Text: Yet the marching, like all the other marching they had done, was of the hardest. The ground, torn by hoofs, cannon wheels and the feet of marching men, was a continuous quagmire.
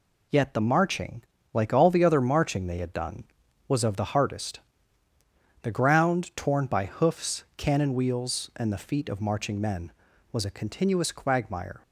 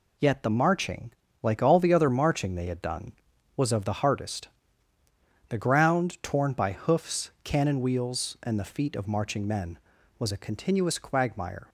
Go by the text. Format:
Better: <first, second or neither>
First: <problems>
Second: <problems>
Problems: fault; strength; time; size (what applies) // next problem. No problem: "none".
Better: neither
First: none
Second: none